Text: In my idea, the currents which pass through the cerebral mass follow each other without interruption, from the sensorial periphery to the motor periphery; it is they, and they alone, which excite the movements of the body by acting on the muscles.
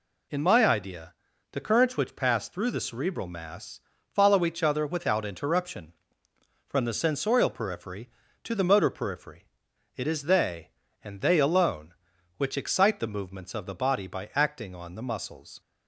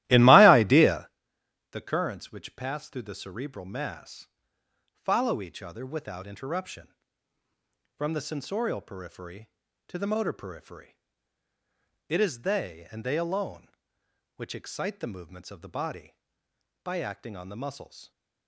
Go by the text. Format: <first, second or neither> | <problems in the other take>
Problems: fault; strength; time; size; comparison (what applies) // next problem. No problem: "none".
first | starts louder than the rest; strong; until 1.2 s; 15.5 dB // pauses between "mass" and "follow"; noticeable; at 4.2 s; 0.66 s long; slight in the first